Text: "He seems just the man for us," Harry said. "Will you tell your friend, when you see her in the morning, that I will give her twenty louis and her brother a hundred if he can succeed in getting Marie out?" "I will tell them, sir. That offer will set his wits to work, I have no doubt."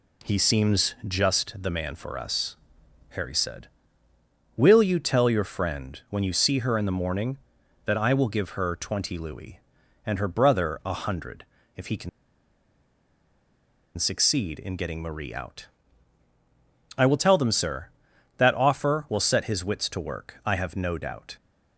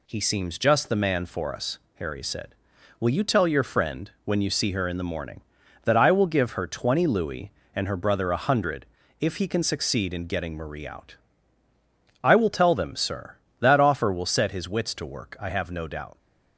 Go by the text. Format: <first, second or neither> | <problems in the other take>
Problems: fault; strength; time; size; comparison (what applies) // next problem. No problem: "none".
second | pauses between "hundred" and "if"; slight; at 11.4 s; 0.30 s long; slight in the second // pauses between "can" and "succeed"; strong; at 12.0 s; 1.8 s long